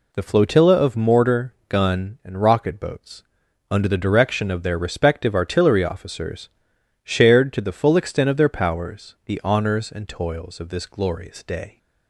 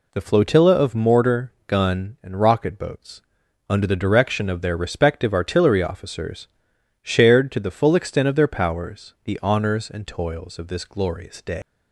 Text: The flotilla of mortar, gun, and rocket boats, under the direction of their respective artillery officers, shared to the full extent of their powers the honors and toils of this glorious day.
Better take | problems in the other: first | leaves "day" unfinished; at 11.6 s; 145 ms

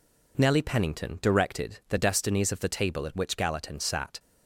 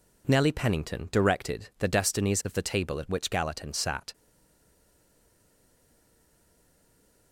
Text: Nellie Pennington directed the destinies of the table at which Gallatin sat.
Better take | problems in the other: first | stays silent after the last word; strong; from 4.1 s on; 3.2 s long

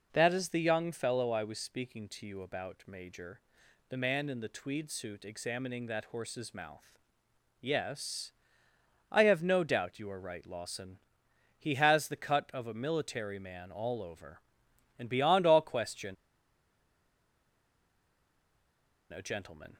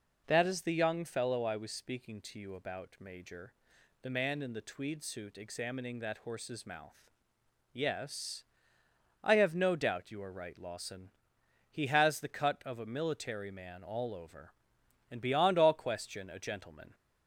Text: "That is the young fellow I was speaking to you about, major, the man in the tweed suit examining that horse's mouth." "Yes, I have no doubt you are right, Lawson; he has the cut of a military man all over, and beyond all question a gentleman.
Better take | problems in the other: second | pauses between "question" and "a"; strong; at 16.1 s; 2.9 s long

